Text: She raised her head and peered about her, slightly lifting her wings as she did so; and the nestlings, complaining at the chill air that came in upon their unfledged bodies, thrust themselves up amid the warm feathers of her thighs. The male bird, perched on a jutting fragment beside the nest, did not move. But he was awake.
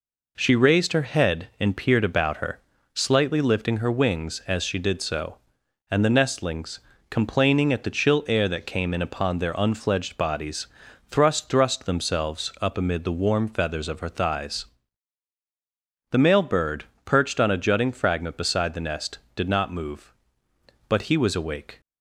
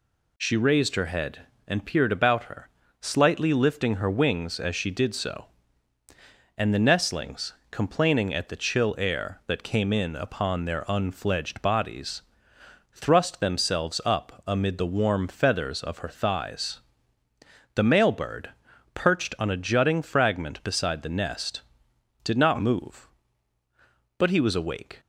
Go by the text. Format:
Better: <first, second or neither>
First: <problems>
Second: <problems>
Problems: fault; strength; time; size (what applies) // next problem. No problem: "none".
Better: second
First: says "thrust" twice; at 11.4 s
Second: none